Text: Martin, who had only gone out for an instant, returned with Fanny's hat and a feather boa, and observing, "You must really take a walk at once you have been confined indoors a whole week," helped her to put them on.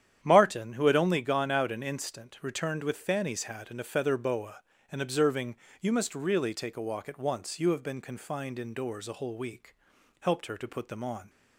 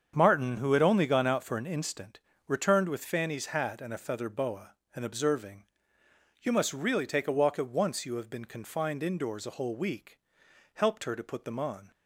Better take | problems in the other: second | starts louder than the rest; strong; until 1.2 s; 9.5 dB; strong in the second // skips "for"; at 1.7 s

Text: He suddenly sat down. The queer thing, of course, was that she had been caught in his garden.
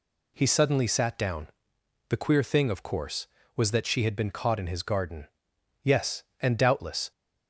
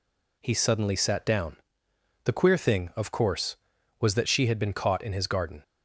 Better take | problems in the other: second | goes on to say "Yes and doubtless"; noticeable; from 5.8 s on; 1.2 s long

